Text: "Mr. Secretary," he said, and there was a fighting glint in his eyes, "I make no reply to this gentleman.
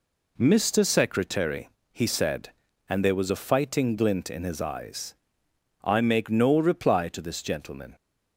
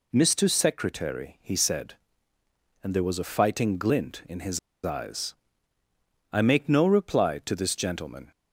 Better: first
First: none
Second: pauses between "his" and "eyes"; slight; at 4.5 s; 0.25 s long

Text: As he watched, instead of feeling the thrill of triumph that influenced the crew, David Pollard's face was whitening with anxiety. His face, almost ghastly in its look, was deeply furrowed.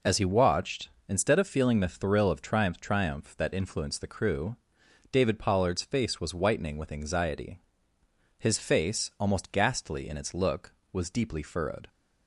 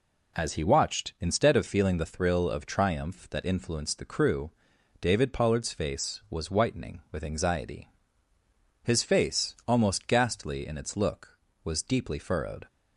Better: second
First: says "triumph" twice; at 2.7 s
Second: none

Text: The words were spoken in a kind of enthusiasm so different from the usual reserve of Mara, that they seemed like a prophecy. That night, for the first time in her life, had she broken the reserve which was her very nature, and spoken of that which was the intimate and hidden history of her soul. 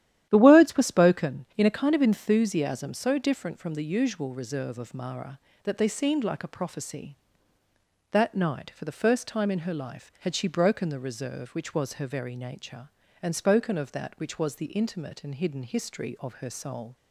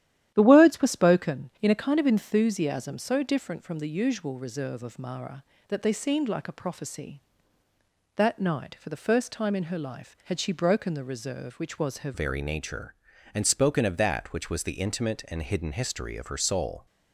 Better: first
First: starts louder than the rest; strong; until 1.3 s; 11.5 dB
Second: starts louder than the rest; strong; until 1.3 s; 11.5 dB // changes voice at "very"; from 12.1 s on; 4.7 s long

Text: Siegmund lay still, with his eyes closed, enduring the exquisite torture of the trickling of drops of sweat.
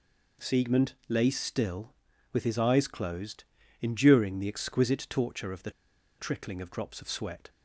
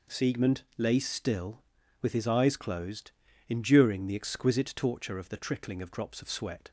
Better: second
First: pauses between "Siegmund" and "lay"; slight; at 0.9 s; 0.16 s long // pauses between "the" and "trickling"; noticeable; at 5.6 s; 0.48 s long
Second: pauses between "Siegmund" and "lay"; slight; at 0.6 s; 0.16 s long

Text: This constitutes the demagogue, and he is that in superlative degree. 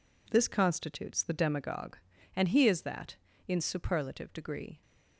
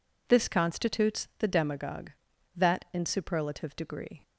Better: first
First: none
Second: skips "and he is"; at 2.3 s

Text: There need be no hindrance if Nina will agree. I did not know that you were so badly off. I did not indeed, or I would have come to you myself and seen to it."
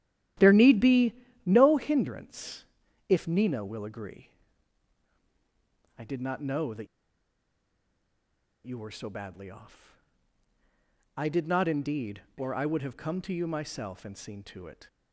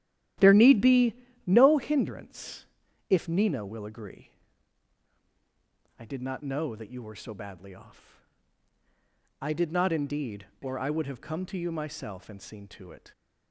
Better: second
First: starts louder than the rest; strong; until 1.6 s; 12.5 dB // pauses between "be" and "no"; slight; at 1.1 s; 0.30 s long // pauses between "hindrance" and "if"; at 2.6 s; 0.44 s long // pauses between "that" and "you"; strong; at 6.8 s; 1.7 s long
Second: starts louder than the rest; strong; until 1.6 s; 12.5 dB // pauses between "be" and "no"; slight; at 1.1 s; 0.30 s long // pauses between "hindrance" and "if"; at 2.6 s; 0.44 s long

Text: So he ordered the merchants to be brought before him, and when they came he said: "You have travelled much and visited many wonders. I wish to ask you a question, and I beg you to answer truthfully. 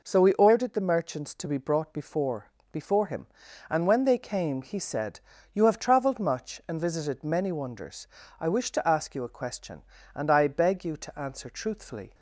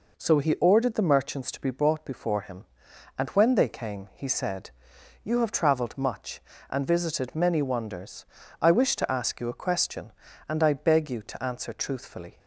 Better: second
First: says "before" twice; at 2.7 s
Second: none

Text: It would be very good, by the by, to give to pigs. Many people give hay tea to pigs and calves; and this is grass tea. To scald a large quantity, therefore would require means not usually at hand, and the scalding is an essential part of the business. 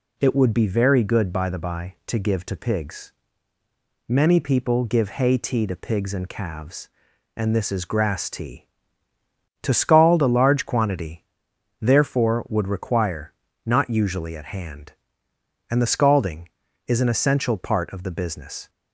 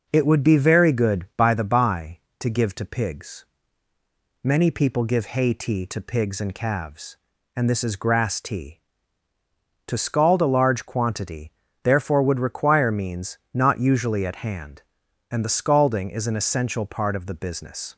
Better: second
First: skips "means"; at 13.4 s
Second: none

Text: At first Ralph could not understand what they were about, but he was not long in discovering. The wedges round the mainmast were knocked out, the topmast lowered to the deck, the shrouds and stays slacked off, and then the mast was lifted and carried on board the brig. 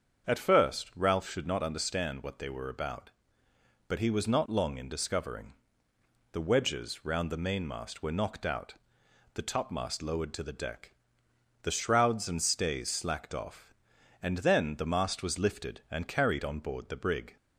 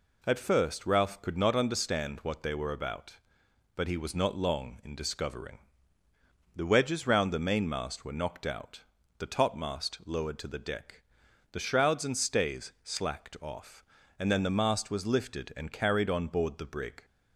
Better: second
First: starts louder than the rest; strong; until 1.3 s; 7 dB // says "should" for "could"; at 1.2 s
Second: none

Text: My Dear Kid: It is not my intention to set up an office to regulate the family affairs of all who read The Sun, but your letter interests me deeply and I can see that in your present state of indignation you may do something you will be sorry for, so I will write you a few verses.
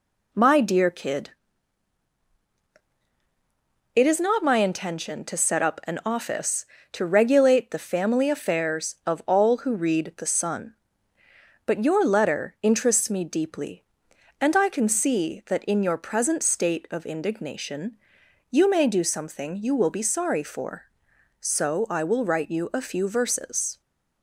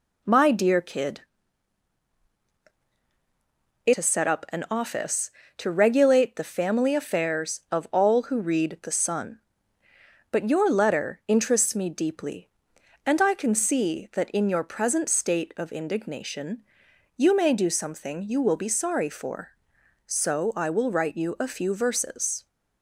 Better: first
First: pauses between "indignation" and "you"; noticeable; at 17.9 s; 0.54 s long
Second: skips "is not my intention"; at 3.9 s // pauses between "indignation" and "you"; noticeable; at 16.6 s; 0.54 s long

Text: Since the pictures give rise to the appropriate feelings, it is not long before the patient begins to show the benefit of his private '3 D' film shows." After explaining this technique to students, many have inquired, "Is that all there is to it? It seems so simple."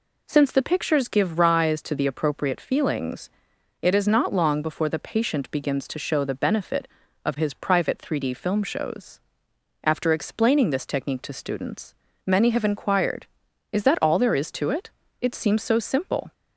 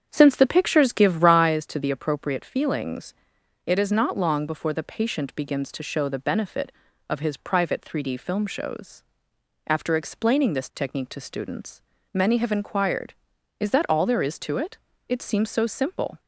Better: first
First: none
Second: starts louder than the rest; strong; until 1.5 s; 8 dB

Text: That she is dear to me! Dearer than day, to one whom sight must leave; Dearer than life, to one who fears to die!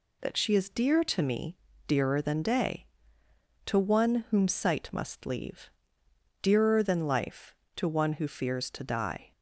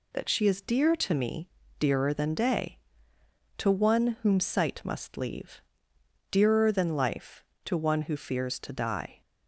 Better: neither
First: none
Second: none

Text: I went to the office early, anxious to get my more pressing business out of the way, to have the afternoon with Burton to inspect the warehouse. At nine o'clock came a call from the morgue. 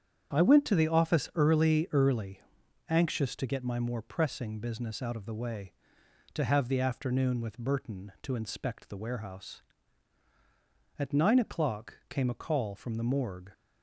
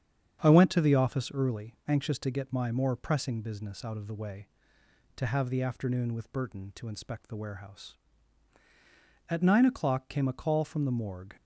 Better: second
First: starts louder than the rest; strong; until 1.4 s; 8.5 dB // says "early" twice; at 1.9 s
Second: starts louder than the rest; strong; until 1.4 s; 7.5 dB

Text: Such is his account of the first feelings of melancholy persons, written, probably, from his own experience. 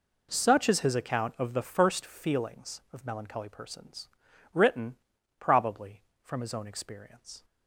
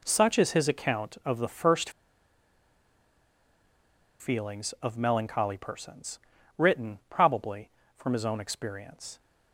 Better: first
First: none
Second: pauses between "first" and "feelings"; strong; at 1.8 s; 2.3 s long

